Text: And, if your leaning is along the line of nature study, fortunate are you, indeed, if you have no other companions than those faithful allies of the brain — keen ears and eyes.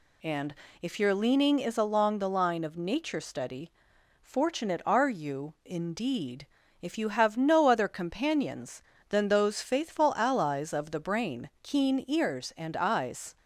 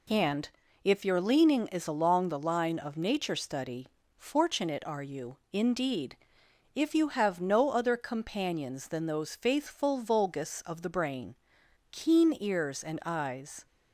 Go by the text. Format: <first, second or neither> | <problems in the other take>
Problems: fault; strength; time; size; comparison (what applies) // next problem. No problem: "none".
first | says "vulgus" for "allies"; at 9.9 s